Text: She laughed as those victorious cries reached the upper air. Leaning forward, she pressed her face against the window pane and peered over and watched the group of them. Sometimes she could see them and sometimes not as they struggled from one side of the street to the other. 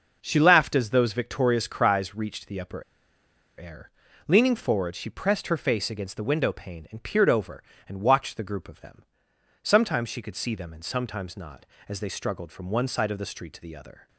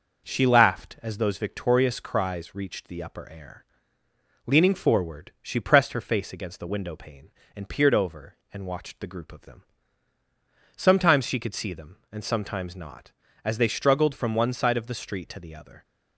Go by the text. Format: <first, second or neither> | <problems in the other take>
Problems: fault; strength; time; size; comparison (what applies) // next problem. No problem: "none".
second | pauses between "upper" and "air"; noticeable; at 2.8 s; 0.76 s long